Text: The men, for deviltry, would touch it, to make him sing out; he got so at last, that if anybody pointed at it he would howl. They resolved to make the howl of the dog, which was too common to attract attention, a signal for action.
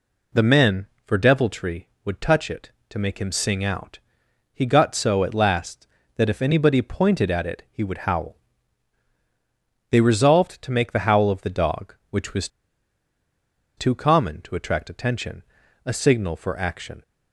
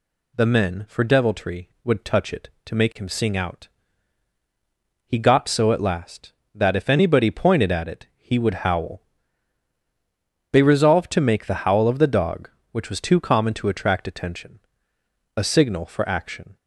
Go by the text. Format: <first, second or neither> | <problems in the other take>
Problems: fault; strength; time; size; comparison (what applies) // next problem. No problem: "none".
second | pauses between "was" and "too"; strong; at 12.4 s; 1.2 s long